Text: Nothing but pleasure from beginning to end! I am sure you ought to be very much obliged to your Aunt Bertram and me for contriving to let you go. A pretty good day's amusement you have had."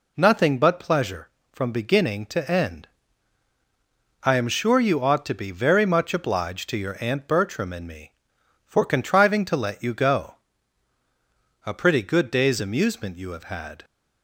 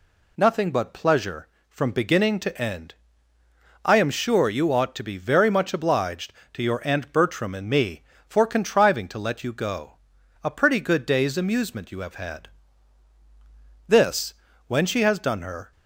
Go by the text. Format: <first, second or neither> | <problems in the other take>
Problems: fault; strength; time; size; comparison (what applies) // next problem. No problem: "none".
first | goes on to say "This when she has done her"; strong; from 13.8 s on; 1.8 s long